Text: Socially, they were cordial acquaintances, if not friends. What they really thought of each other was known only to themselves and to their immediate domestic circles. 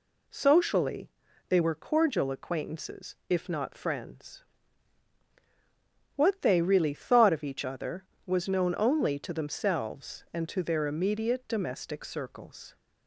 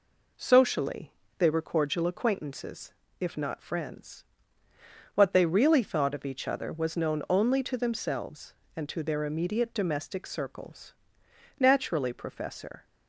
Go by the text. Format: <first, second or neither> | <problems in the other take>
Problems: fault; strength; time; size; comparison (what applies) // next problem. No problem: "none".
first | goes on to say "Naturally Professor"; noticeable; from 11.5 s on; 1.2 s long